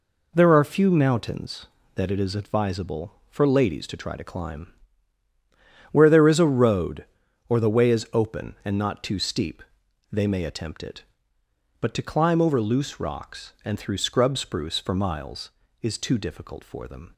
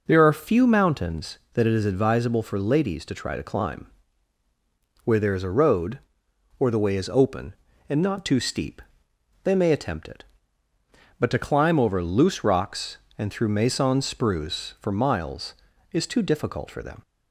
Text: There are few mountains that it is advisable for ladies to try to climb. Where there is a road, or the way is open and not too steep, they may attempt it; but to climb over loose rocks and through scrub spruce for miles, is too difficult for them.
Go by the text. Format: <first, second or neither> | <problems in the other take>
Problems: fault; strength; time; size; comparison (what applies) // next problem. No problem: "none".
first | says "maison" for "scrub"; at 13.4 s